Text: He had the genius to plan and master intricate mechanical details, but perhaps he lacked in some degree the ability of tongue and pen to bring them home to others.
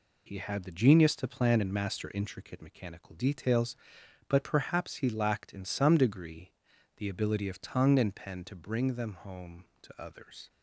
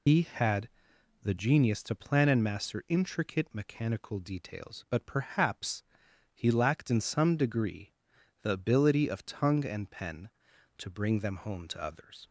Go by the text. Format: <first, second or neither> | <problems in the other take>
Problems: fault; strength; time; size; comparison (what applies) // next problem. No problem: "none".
first | loses the start of "He"; at 0.0 s; 115 ms // pauses between "had" and "the"; noticeable; at 0.6 s; 0.54 s long // pauses between "perhaps" and "he"; noticeable; at 5.8 s; 0.52 s long // pauses between "degree" and "the"; noticeable; at 7.9 s; 0.48 s long; noticeable in the first